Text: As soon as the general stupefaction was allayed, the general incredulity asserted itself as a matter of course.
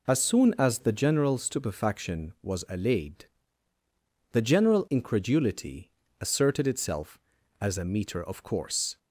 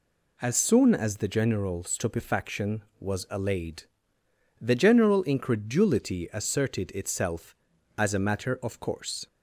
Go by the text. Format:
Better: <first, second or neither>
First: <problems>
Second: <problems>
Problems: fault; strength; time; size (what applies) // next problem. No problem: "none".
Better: second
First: pauses between "incredulity" and "asserted"; slight; at 5.9 s; 0.28 s long // says "meter" for "matter"; at 7.8 s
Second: none